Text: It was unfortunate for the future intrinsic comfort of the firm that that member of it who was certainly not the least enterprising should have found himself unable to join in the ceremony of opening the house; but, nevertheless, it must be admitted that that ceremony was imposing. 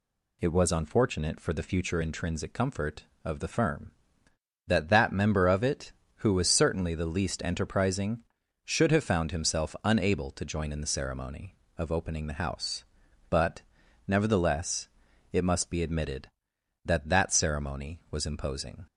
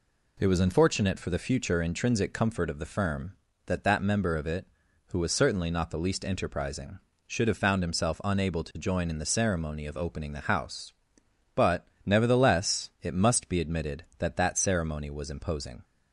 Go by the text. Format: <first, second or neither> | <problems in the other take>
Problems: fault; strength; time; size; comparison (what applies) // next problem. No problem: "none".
second | skips "not"; at 6.9 s